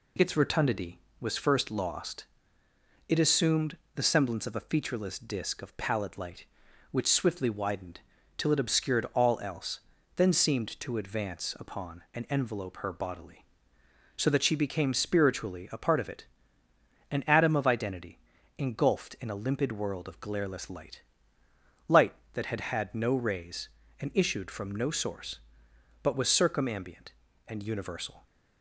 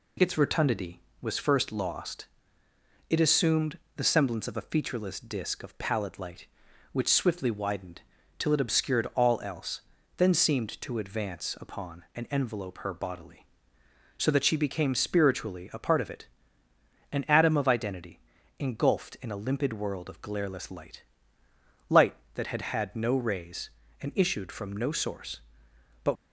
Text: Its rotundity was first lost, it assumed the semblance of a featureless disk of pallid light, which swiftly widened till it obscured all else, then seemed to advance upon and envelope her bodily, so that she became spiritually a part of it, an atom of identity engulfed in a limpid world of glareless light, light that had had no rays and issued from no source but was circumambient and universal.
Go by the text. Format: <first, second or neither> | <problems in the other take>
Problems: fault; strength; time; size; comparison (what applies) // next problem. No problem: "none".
first | pauses between "assumed" and "the"; slight; at 3.7 s; 0.16 s long; slight in the first // pauses between "widened" and "till"; slight; at 8.0 s; 0.36 s long; slight in the first // pauses between "identity" and "engulfed"; at 18.1 s; 0.40 s long; also in the first // stops before "was circumambient and universal"; at 26.1 s